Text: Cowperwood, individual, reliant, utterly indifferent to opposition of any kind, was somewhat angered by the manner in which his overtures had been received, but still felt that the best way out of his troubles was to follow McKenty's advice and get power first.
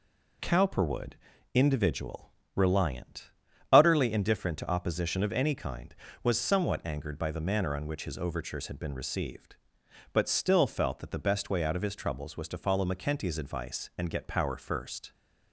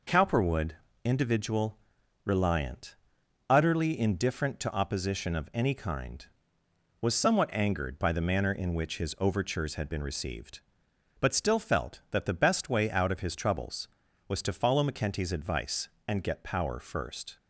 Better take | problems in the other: second | says "on" for "in"; at 7.7 s

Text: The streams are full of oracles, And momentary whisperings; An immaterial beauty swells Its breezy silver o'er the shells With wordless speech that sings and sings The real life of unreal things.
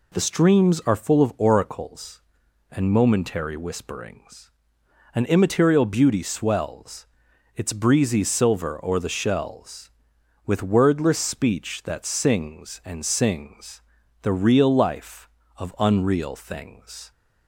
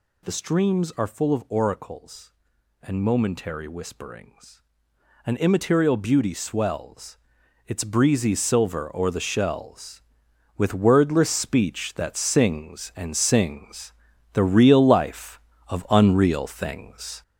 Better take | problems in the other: first | gets louder; noticeable; throughout; 5 dB // pauses between "swells" and "Its"; noticeable; at 7.1 s; 0.48 s long; noticeable in the first // pauses between "sings" and "The"; at 13.9 s; 0.40 s long; also in the first

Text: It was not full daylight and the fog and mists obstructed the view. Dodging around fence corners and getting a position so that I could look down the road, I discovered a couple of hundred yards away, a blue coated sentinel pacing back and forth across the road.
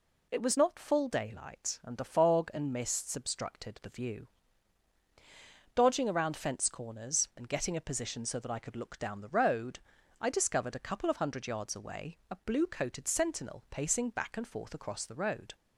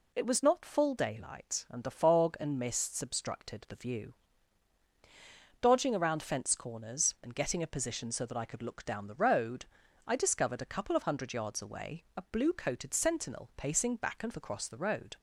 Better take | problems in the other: first | skips "forth"; at 14.3 s

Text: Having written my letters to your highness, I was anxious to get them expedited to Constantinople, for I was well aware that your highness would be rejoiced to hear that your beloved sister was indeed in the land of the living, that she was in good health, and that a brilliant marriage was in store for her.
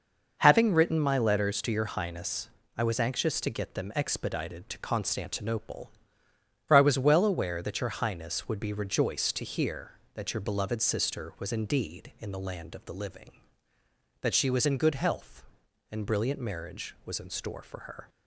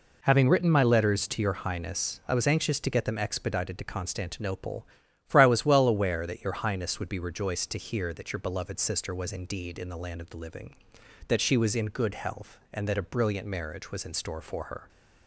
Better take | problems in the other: second | skips "that a"; at 16.0 s

